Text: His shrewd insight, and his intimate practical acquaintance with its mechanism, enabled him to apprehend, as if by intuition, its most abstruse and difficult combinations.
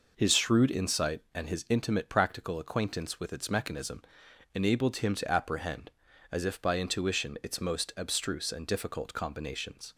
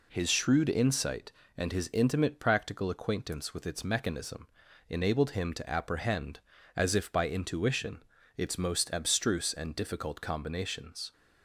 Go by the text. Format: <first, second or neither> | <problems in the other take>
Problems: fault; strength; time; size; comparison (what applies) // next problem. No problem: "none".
neither | none